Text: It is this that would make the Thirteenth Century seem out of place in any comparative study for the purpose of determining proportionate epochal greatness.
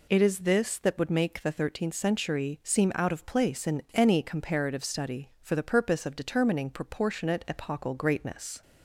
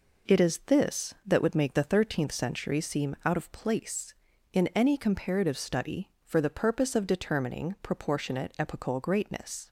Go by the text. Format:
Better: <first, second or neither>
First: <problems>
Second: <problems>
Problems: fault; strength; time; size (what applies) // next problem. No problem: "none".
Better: neither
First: none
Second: none